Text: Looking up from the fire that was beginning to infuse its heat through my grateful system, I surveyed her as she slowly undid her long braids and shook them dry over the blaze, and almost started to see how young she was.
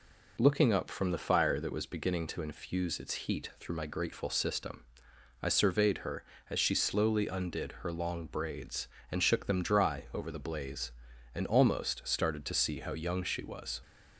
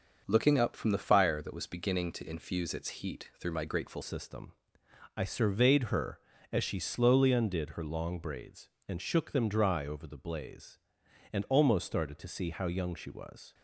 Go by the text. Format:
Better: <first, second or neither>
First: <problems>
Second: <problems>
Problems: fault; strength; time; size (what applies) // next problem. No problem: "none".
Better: first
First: none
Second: starts louder than the rest; until 1.2 s; 6 dB // changes voice at "system"; from 4.0 s on; 9.5 s long